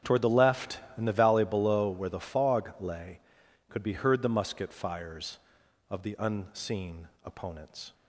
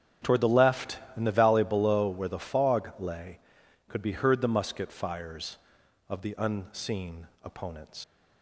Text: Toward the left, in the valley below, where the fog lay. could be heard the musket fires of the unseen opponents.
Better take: first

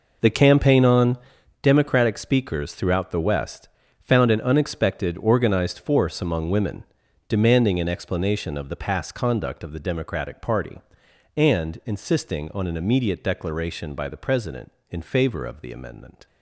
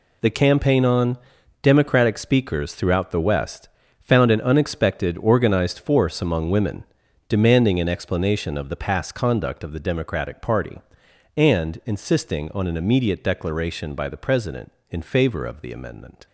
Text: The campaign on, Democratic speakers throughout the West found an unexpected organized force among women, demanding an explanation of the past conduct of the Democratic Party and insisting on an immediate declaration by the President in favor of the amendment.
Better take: second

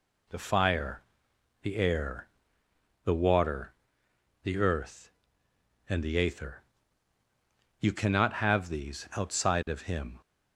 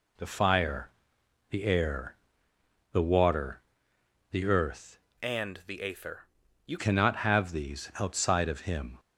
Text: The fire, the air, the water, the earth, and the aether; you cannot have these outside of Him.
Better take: first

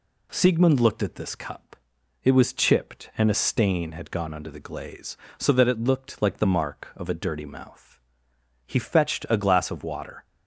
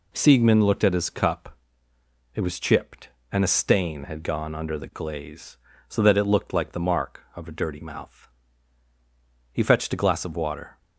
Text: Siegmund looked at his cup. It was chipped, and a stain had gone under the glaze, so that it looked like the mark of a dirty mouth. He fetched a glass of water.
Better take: second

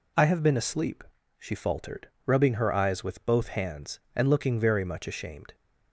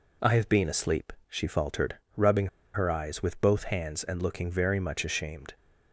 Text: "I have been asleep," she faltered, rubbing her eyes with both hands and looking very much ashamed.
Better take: first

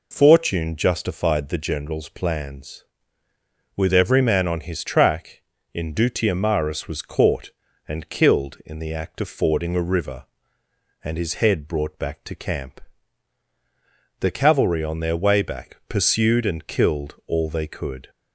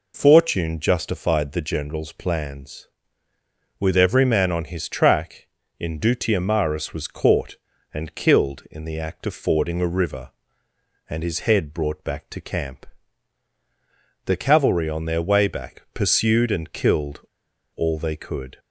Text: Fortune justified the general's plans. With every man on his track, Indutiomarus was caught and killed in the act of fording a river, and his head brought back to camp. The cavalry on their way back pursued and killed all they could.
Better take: first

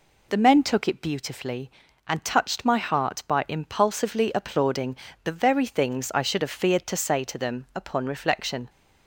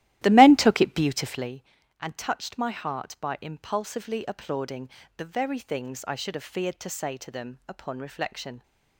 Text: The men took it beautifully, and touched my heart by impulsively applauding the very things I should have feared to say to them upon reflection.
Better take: first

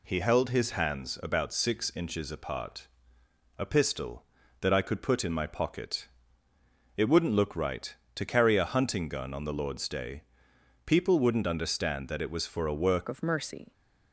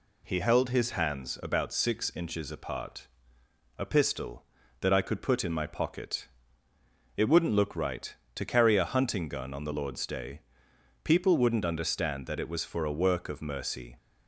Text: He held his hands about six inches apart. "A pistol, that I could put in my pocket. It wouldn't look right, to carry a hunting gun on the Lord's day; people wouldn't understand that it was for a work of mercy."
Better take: second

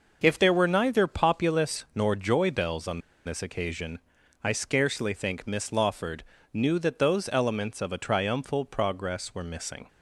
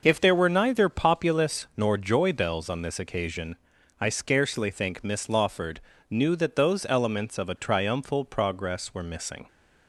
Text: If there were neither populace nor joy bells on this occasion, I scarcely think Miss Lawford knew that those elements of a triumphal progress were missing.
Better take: second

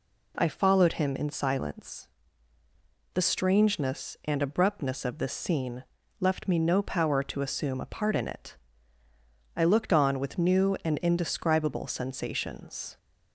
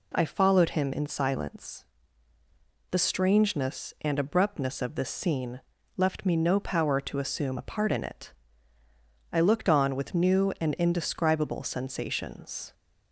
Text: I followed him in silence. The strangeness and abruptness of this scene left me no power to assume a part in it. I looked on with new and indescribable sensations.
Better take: neither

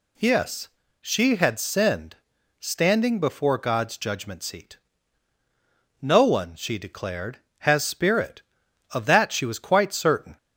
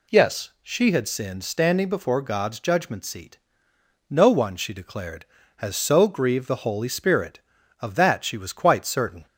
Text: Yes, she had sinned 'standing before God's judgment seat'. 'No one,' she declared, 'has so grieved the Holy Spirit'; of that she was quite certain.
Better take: second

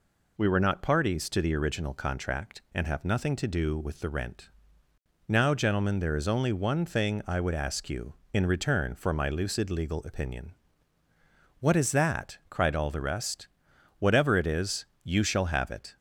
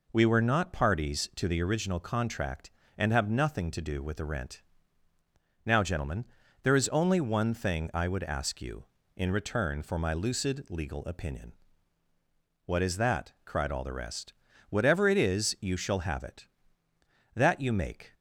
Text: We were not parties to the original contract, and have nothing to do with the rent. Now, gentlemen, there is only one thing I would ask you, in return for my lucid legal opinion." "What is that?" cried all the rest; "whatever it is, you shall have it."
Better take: first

